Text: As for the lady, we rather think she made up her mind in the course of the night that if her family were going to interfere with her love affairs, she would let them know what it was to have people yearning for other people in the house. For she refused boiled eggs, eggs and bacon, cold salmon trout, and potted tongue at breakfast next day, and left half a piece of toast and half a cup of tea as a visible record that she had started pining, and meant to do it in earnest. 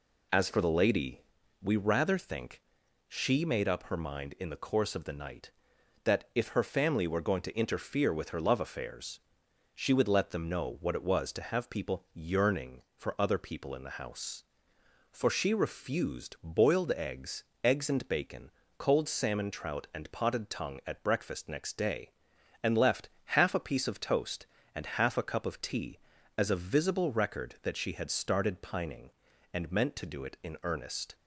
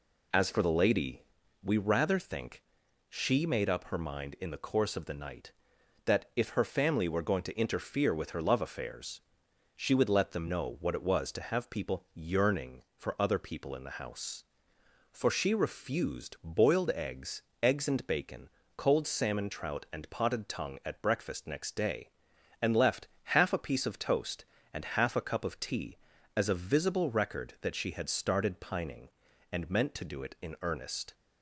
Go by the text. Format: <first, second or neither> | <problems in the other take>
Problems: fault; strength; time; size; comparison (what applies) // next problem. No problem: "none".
neither | pauses between "think" and "she"; noticeable; the same in both // pauses between "left" and "half"; slight; the same in both